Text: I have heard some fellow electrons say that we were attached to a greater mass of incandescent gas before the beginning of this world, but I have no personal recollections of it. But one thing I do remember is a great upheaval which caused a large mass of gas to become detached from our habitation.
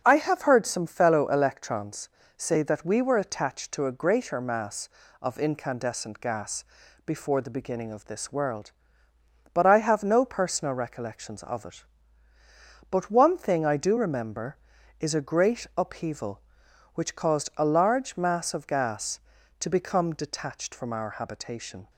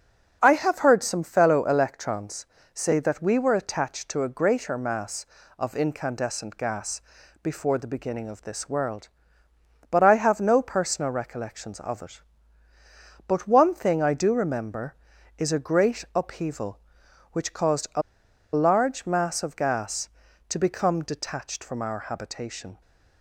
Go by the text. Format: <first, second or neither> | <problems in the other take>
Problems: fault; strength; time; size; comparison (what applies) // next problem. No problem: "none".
first | starts louder than the rest; until 1.4 s; 6.5 dB; also in the first // pauses between "electrons" and "say"; slight; at 2.4 s; 0.28 s long; slight in the first // pauses between "gas" and "before"; at 7.0 s; 0.42 s long; also in the first // pauses between "a" and "large"; noticeable; at 18.0 s; 0.52 s long